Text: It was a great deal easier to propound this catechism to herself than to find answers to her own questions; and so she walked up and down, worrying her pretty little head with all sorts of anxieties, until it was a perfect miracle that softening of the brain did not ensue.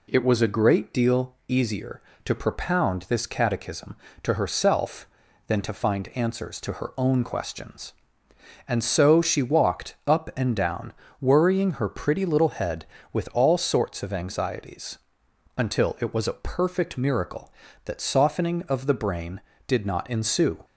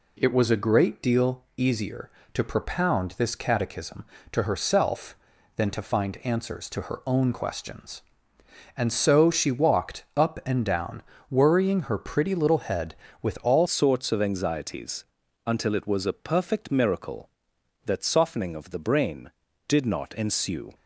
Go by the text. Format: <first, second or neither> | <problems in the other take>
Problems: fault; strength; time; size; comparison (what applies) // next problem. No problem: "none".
first | changes voice at "sorts"; from 13.6 s on; 7.1 s long